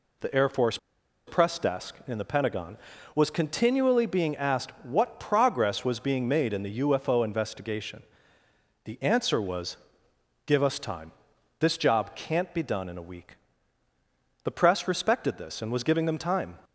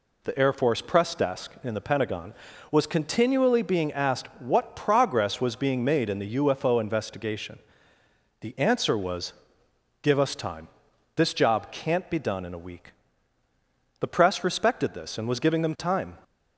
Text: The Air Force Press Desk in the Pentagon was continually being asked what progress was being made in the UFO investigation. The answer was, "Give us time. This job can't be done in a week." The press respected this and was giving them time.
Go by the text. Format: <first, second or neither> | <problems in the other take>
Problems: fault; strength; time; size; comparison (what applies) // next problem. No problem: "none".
second | pauses between "Force" and "Press"; noticeable; at 0.7 s; 0.48 s long